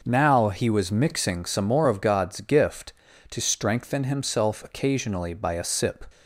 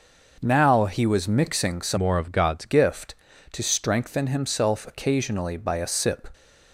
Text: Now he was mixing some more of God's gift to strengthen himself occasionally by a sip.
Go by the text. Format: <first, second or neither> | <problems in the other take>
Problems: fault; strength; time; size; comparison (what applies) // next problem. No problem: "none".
first | changes voice from "more" to "God's"; from 1.9 to 2.6 s; 0.7 s long